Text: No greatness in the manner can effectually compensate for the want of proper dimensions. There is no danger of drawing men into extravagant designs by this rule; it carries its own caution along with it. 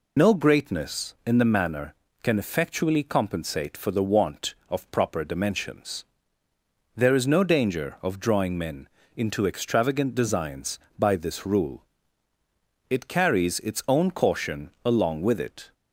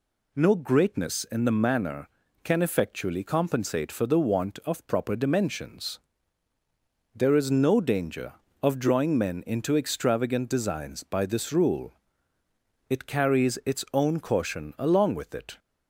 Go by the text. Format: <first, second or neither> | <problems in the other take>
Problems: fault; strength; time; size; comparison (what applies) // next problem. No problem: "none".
second | loses the start of "No"; at 0.1 s; 60 ms // pauses between "men" and "into"; slight; at 8.8 s; 0.30 s long